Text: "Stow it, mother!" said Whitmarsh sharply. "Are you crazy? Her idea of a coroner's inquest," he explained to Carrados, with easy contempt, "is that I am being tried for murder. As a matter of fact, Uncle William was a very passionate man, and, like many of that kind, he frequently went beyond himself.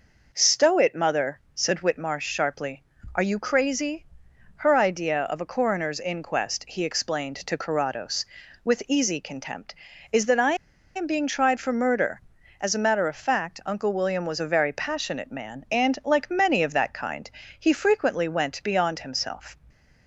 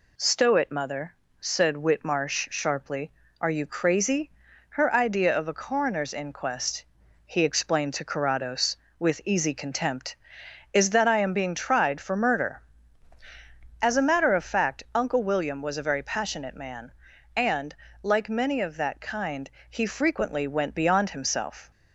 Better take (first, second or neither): second